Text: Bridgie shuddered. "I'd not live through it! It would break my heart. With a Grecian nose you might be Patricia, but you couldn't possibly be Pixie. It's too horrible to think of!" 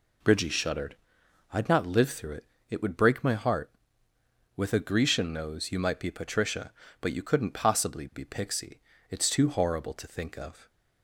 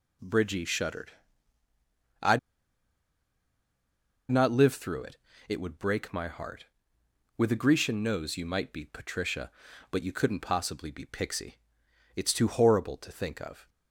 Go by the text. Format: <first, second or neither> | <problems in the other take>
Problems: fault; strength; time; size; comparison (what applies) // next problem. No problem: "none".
first | pauses between "I'd" and "not"; strong; at 2.3 s; 1.9 s long